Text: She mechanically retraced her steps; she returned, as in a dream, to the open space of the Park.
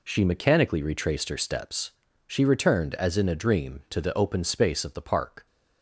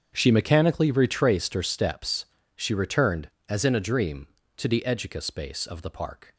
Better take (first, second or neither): first